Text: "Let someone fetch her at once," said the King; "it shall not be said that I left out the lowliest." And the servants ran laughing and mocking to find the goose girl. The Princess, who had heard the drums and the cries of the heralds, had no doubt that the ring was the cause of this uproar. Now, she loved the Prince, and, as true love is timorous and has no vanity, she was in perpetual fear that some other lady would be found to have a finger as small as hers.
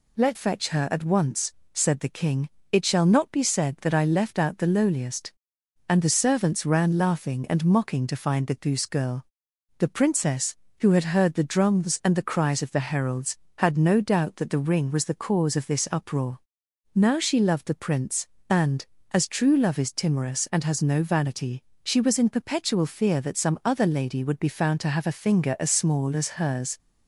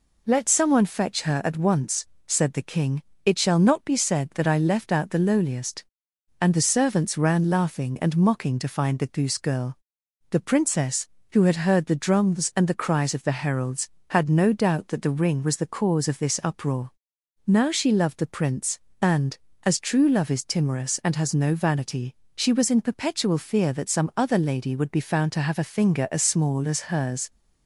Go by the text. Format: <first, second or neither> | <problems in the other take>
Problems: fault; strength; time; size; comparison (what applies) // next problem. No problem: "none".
second | skips "someone"; at 0.3 s